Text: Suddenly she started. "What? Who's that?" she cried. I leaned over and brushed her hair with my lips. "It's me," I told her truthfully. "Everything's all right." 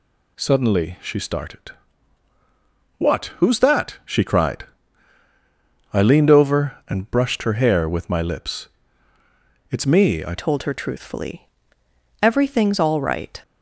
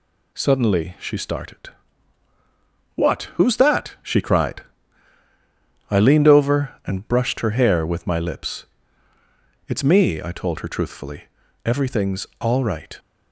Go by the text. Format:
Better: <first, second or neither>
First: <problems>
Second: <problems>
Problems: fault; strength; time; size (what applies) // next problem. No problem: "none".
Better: second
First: changes voice at "told"; from 10.3 s on; 3.0 s long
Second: none